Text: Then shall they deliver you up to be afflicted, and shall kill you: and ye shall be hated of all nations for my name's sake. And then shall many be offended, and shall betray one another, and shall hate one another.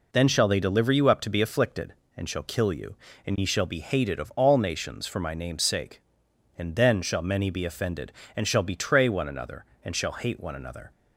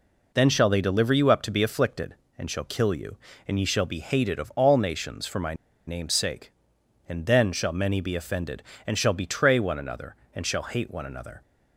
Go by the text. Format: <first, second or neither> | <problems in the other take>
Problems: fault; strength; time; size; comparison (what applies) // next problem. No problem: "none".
first | pauses between "my" and "name's"; slight; at 5.5 s; 0.32 s long